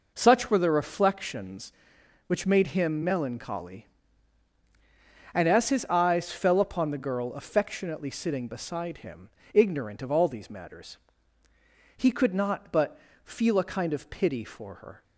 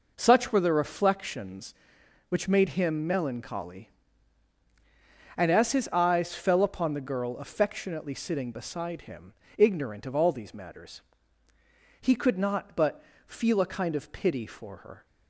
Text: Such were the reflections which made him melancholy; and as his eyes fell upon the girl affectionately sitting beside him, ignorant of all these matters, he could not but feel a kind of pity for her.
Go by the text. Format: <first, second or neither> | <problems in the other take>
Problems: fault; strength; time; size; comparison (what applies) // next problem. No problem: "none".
neither | pauses between "but" and "feel"; slight; the same in both